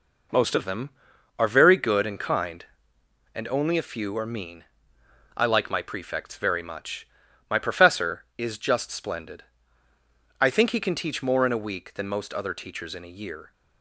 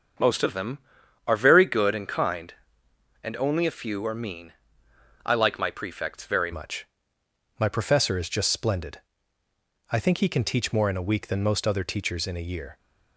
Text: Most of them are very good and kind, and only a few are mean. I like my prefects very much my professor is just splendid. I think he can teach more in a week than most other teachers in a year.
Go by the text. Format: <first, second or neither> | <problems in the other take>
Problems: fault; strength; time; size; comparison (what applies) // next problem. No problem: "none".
first | starts louder than the rest; until 1.6 s; 7 dB // changes voice at "much"; from 6.5 s on; 6.2 s long // pauses between "much" and "my"; noticeable; at 6.8 s; 0.74 s long; also in the first